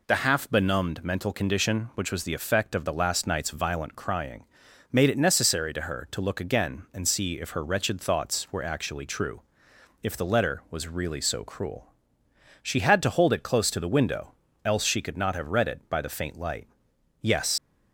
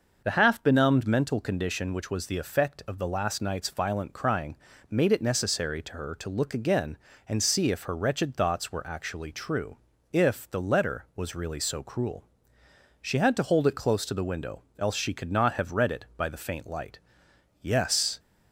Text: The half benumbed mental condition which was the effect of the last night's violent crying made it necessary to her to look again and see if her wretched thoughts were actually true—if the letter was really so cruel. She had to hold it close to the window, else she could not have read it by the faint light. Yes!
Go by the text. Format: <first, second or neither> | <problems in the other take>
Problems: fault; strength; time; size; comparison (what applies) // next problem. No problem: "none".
second | pauses between "crying" and "made"; noticeable; at 4.4 s; 0.48 s long; slight in the second // leaves "Yes" unfinished; at 17.5 s; 120 ms